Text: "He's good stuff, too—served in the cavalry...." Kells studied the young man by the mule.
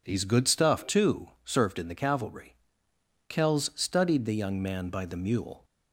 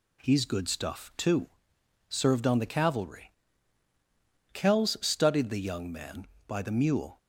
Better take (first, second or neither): first